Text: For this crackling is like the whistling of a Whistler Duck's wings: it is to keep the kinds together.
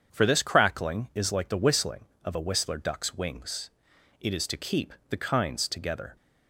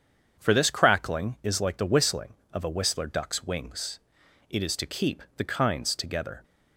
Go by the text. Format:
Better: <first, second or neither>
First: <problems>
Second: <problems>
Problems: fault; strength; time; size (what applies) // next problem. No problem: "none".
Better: neither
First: starts louder than the rest; strong; until 1.1 s; 7.5 dB // pauses between "keep" and "the"; slight; at 4.9 s; 0.18 s long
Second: starts louder than the rest; strong; until 1.4 s; 7.5 dB // pauses between "keep" and "the"; slight; at 5.2 s; 0.16 s long